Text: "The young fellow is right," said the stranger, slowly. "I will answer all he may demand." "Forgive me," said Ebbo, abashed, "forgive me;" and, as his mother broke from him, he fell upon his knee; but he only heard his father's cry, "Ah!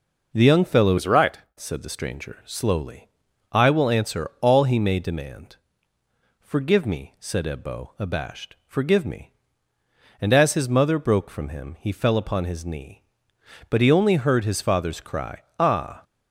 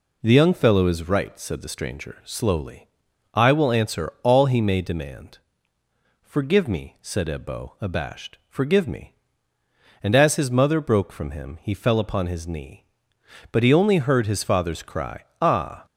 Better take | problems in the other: second | changes voice from "is" to "right"; from 0.9 to 1.3 s; 0.4 s long

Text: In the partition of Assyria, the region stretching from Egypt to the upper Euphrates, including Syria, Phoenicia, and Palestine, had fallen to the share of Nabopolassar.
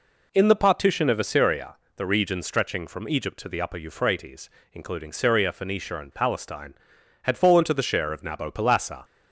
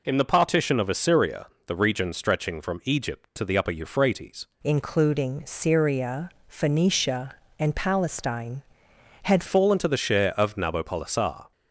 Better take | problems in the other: first | changes voice from "including" to "had"; from 4.6 to 9.4 s; 4.8 s long

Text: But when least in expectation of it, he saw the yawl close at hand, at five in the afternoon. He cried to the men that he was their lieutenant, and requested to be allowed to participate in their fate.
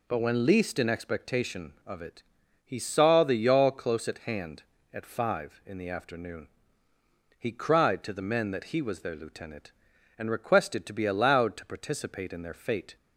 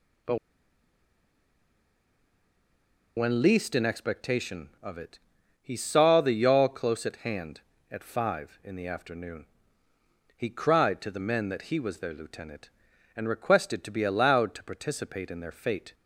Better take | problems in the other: first | pauses between "But" and "when"; strong; at 0.3 s; 2.7 s long

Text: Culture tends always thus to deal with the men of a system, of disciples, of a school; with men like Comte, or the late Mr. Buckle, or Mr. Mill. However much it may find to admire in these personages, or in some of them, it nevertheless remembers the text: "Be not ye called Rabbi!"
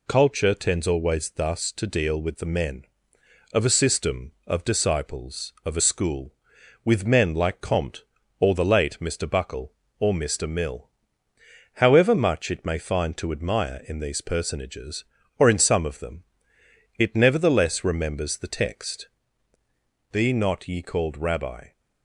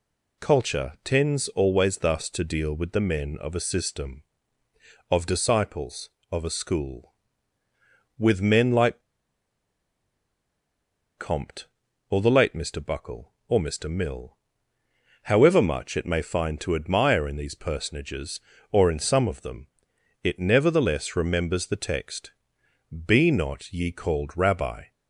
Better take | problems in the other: first | pauses between "like" and "Comte"; strong; at 9.0 s; 2.1 s long

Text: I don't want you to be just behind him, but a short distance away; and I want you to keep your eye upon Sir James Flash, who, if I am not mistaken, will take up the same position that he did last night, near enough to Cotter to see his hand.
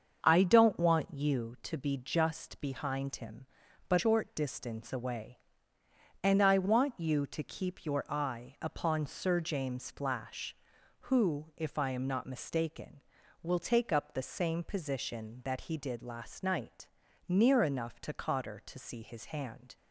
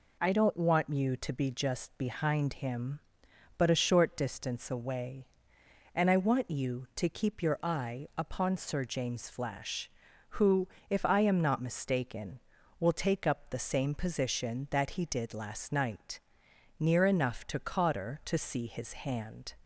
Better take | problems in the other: second | starts louder than the rest; until 1.2 s; 6.5 dB // skips "a"; at 3.9 s

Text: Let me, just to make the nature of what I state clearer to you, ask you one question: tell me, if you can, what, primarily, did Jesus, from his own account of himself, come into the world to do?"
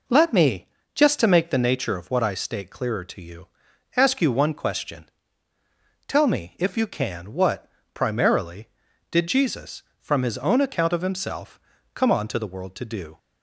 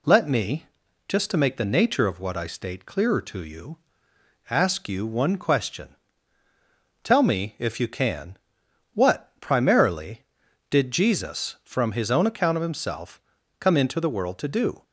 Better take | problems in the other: second | says "onto" for "into"; at 12.1 s

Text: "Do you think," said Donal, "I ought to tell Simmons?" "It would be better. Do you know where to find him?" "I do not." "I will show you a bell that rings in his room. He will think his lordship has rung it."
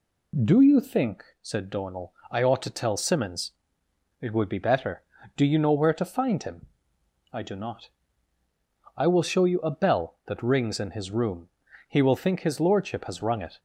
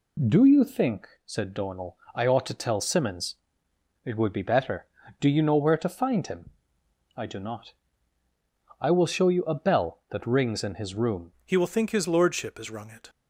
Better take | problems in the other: first | changes voice at "He"; from 11.4 s on; 1.6 s long

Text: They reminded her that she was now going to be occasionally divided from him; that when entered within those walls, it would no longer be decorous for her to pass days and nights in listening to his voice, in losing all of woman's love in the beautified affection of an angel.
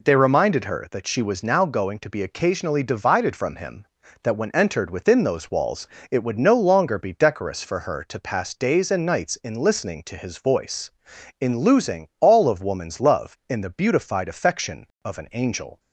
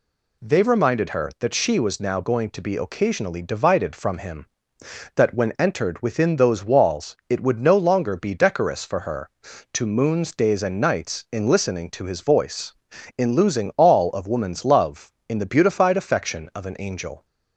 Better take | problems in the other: first | says "moons" for "pass"; at 9.8 s

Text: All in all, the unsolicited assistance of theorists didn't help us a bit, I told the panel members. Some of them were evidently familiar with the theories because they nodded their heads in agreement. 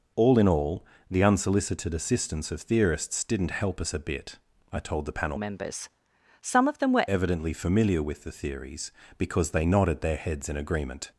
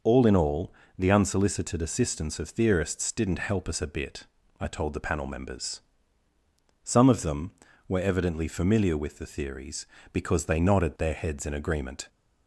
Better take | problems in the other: second | changes voice from "members" to "were"; from 5.3 to 7.0 s; 1.7 s long

